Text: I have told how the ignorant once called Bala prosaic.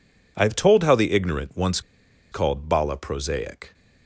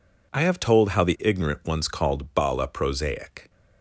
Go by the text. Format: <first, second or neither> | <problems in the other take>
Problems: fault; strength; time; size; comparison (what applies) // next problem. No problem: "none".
second | pauses between "once" and "called"; noticeable; at 1.8 s; 0.51 s long